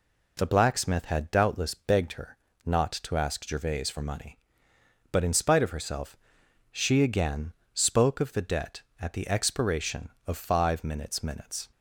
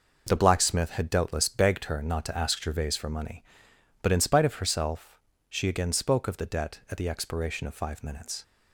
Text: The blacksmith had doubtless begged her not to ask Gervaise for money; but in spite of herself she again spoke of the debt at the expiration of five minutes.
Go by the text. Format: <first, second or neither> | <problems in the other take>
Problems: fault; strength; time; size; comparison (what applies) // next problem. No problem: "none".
second | pauses between "her" and "not"; slight; at 2.3 s; 0.28 s long // pauses between "herself" and "she"; noticeable; at 6.1 s; 0.56 s long; slight in the second // pauses between "again" and "spoke"; slight; at 7.5 s; 0.18 s long // says "minutes" twice; at 11.2 s